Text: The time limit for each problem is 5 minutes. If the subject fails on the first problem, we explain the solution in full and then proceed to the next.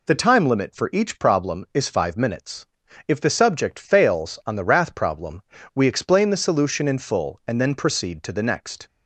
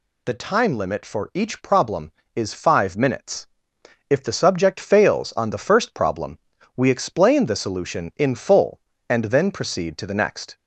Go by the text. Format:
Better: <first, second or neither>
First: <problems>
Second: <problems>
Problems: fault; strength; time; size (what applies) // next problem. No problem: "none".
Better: second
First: says "wrath" for "first"; at 4.6 s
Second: none